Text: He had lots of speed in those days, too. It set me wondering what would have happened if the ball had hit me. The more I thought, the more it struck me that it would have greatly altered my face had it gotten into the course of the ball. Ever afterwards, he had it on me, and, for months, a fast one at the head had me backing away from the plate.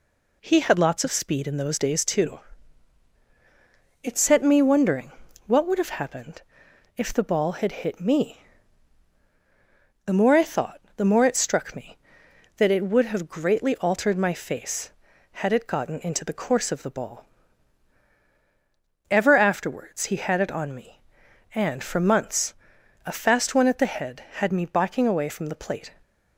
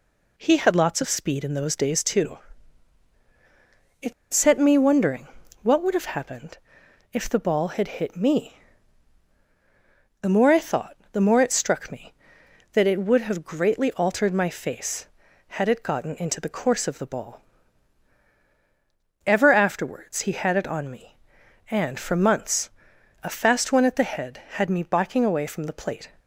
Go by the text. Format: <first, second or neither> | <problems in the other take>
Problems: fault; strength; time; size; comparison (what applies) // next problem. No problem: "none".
first | pauses between "It" and "set"; slight; at 4.1 s; 0.20 s long // pauses between "wondering" and "what"; slight; at 5.2 s; 0.34 s long; slight in the first // pauses between "happened" and "if"; noticeable; at 6.5 s; 0.54 s long; noticeable in the first